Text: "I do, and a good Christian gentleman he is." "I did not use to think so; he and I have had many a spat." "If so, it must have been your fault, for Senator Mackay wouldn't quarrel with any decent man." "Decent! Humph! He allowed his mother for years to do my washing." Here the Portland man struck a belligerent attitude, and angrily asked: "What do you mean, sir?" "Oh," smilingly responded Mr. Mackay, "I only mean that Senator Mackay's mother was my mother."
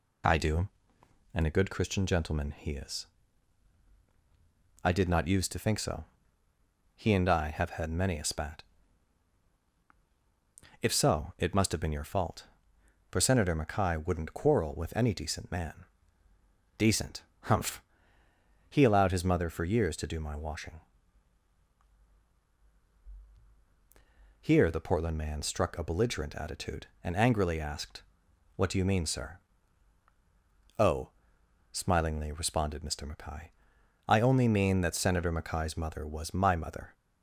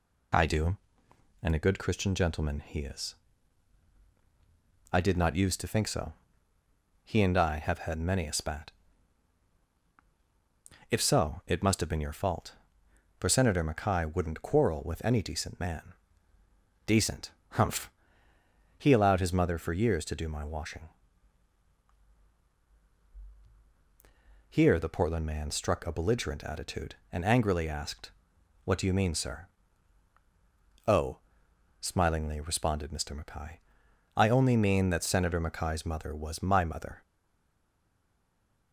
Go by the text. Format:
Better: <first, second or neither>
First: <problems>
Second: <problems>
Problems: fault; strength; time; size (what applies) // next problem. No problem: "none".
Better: first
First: none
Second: stays silent after the last word; noticeable; from 37.0 s on; 1.7 s long